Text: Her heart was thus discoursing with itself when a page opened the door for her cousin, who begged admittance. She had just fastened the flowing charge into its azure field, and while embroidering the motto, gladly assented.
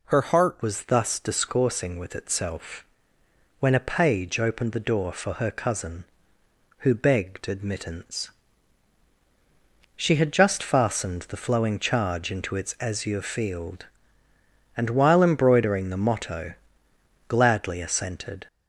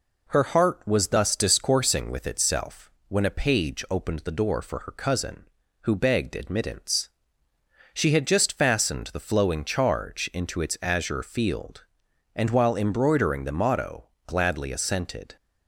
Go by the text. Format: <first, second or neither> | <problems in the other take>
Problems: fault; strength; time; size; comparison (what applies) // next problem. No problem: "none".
second | changes voice at "was"; from 0.6 s on; 17.8 s long // pauses between "itself" and "when"; noticeable; at 2.8 s; 0.78 s long; slight in the second